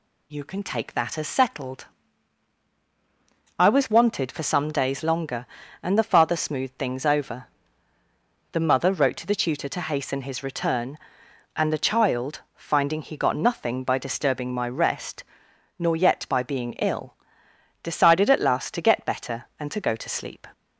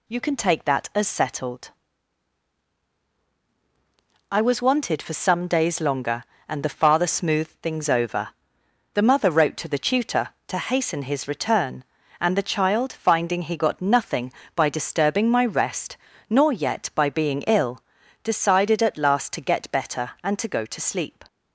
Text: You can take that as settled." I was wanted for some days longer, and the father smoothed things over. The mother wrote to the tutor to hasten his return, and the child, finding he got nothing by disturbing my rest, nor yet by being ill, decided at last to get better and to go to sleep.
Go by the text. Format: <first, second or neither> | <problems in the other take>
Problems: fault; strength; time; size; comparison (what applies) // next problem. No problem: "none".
neither | none